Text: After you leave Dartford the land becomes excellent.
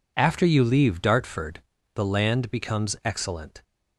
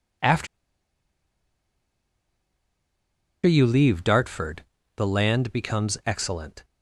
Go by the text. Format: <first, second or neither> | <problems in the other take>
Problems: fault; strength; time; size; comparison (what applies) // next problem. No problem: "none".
first | pauses between "After" and "you"; strong; at 0.4 s; 2.9 s long // pauses between "Dartford" and "the"; slight; at 4.6 s; 0.34 s long; slight in the first